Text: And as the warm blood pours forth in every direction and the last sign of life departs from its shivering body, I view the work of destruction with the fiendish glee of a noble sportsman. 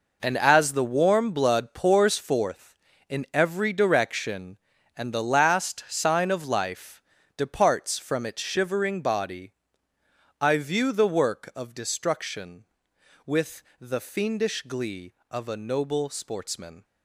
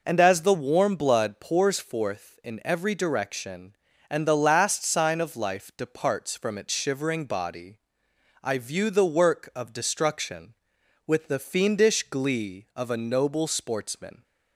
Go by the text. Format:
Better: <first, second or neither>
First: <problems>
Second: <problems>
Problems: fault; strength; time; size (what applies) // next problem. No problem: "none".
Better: second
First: gets quieter; strong; throughout; 11 dB // pauses between "life" and "departs"; slight; at 7.0 s; 0.34 s long // pauses between "with" and "the"; slight; at 13.6 s; 0.18 s long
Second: none